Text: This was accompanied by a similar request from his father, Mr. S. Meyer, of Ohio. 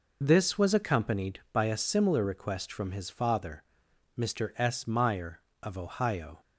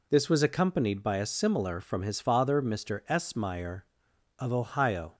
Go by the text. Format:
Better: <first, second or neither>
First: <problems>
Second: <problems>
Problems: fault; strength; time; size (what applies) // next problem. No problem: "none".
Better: first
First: none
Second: skips "request"; at 1.8 s